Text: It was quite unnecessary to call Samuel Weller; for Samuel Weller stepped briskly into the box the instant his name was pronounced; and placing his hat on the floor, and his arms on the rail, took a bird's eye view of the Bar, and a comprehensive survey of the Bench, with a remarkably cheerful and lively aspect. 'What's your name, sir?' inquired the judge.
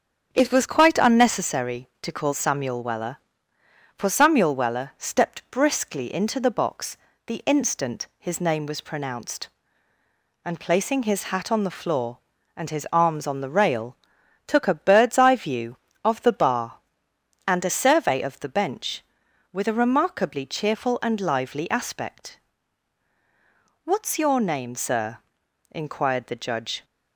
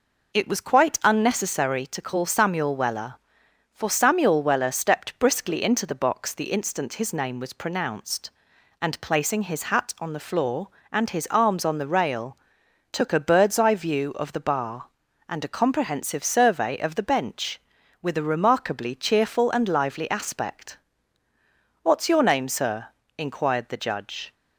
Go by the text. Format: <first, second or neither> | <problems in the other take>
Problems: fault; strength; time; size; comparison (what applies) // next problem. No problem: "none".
second | starts louder than the rest; strong; until 1.3 s; 8 dB // pauses between "box" and "the"; slight; at 6.9 s; 0.30 s long // skips "comprehensive"; at 17.8 s